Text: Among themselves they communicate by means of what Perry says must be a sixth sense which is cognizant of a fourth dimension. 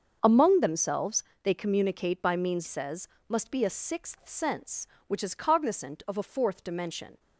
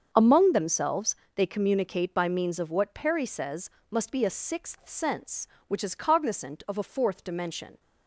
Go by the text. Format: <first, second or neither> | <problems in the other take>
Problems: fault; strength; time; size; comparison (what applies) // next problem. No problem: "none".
second | starts louder than the rest; until 1.2 s; 6.5 dB; also in the second // pauses between "themselves" and "they"; slight; at 1.2 s; 0.20 s long; slight in the second // skips "of what Perry"; at 2.6 s // pauses between "says" and "must"; slight; at 3.0 s; 0.20 s long; slight in the second